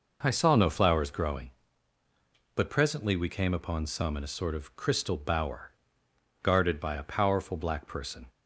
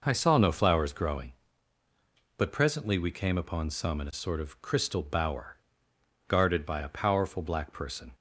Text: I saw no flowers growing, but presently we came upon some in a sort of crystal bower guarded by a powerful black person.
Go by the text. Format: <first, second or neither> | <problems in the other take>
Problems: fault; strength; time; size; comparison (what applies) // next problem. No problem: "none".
neither | pauses between "bower" and "guarded"; noticeable; the same in both